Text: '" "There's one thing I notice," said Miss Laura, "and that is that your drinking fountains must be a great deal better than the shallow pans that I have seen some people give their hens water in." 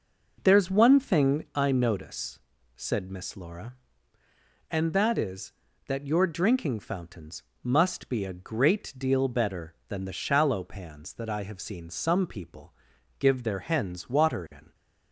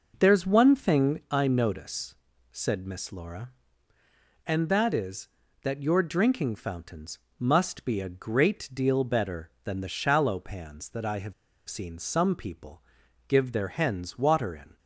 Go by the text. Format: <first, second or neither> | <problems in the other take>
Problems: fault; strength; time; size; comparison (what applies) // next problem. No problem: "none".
first | pauses between "fountains" and "must"; slight; at 7.1 s; 0.18 s long; slight in the first // pauses between "have" and "seen"; slight; at 11.3 s; 0.34 s long // pauses between "people" and "give"; noticeable; at 12.8 s; 0.46 s long; noticeable in the first